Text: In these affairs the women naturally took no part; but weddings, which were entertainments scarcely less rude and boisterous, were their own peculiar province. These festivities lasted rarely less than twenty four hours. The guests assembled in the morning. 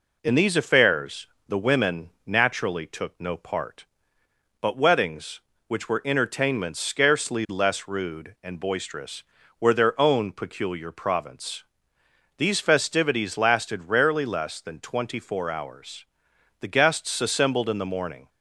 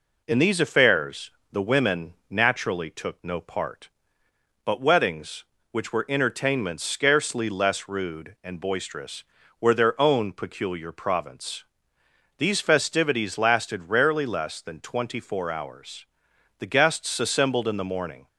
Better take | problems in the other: neither | pauses between "affairs" and "the"; slight; the same in both // pauses between "women" and "naturally"; slight; the same in both

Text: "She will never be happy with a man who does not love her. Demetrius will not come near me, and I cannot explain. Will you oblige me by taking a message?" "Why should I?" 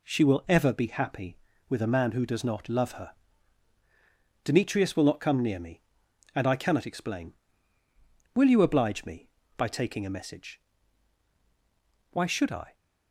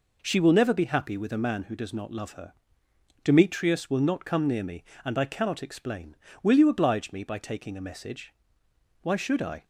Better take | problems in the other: second | says "ever" for "never"; at 0.4 s

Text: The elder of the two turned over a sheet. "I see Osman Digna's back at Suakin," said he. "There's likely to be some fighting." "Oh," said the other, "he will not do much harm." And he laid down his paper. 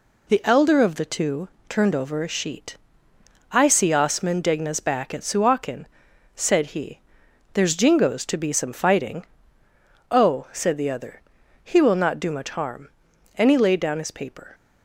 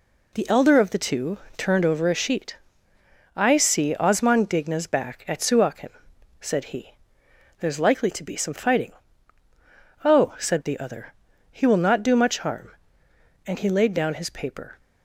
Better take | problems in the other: second | pauses between "two" and "turned"; slight; at 1.4 s; 0.20 s long; slight in the second // says "jingoes" for "likely"; at 7.7 s

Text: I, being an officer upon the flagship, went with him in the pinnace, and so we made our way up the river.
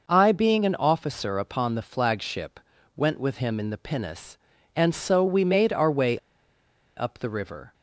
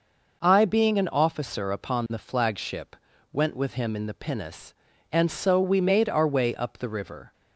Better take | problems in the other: second | pauses between "way" and "up"; noticeable; at 6.1 s; 0.78 s long

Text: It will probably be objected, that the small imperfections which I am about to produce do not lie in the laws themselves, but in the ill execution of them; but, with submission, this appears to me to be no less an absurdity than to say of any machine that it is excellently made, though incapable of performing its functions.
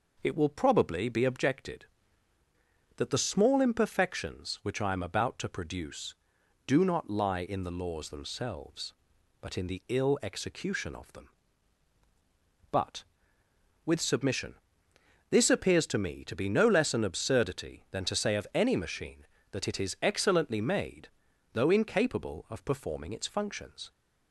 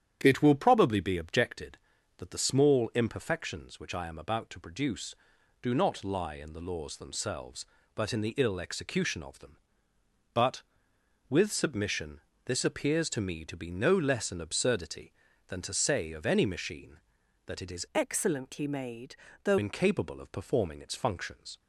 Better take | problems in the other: first | starts louder than the rest; strong; until 1.2 s; 9.5 dB // changes voice from "excellently" to "though"; from 17.9 to 19.5 s; 1.6 s long

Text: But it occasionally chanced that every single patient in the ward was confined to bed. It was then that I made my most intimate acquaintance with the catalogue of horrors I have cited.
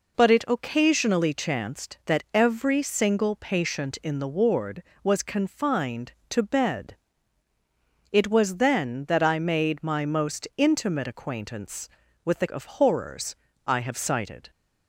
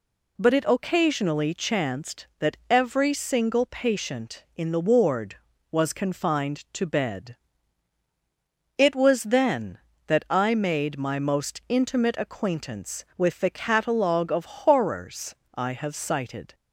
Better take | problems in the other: second | skips "catalogue"; at 12.4 s // pauses between "horrors" and "I"; slight; at 13.3 s; 0.28 s long; slight in the second

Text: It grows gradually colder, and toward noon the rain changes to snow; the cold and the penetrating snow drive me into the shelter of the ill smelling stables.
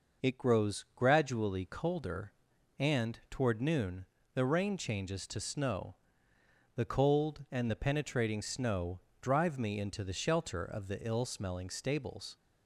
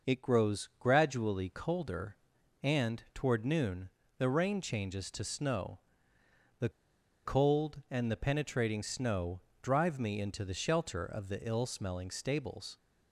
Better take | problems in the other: first | pauses between "noon" and "the"; slight; at 3.8 s; 0.28 s long; slight in the first // pauses between "the" and "cold"; noticeable; at 6.6 s; 0.55 s long // pauses between "snow" and "drive"; slight; at 9.4 s; 0.22 s long; slight in the first

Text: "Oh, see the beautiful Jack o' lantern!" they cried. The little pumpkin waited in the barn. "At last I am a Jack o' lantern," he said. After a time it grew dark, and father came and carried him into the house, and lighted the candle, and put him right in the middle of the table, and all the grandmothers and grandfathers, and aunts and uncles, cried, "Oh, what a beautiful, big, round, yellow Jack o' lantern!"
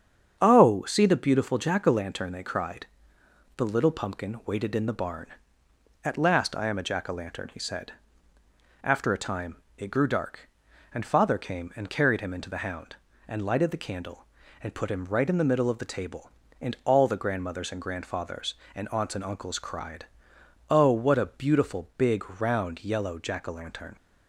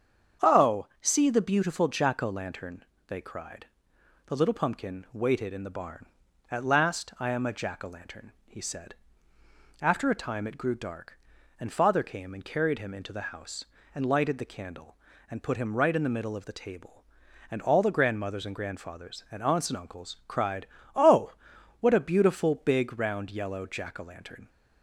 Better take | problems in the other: second | starts louder than the rest; strong; until 1.4 s; 7.5 dB; strong in the second // pauses between "time" and "it"; slight; at 9.6 s; 0.16 s long // says "hound" for "house"; at 12.6 s

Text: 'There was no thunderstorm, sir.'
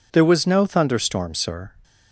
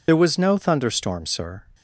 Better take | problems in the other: first | loses the start of "There"; at 0.0 s; 50 ms

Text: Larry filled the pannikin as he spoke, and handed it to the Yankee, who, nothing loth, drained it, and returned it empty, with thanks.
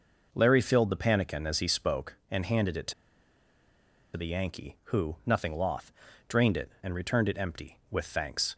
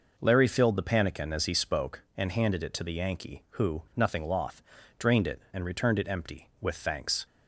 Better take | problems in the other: second | pauses between "to" and "the"; at 2.9 s; 1.2 s long

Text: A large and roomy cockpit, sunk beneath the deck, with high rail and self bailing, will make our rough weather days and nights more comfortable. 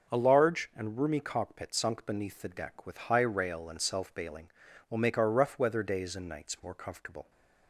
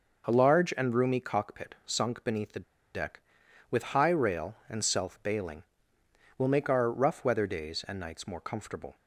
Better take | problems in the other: first | pauses between "the" and "deck"; slight; at 2.6 s; 0.31 s long

